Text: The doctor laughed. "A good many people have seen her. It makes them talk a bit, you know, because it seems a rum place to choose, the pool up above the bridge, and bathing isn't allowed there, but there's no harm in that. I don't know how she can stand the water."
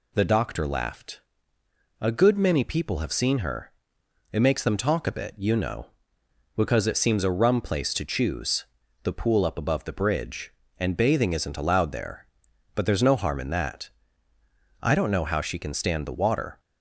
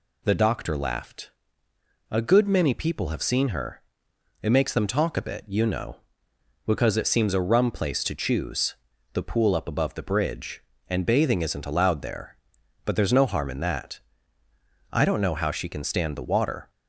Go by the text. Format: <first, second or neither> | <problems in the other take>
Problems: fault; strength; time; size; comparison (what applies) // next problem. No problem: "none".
neither | none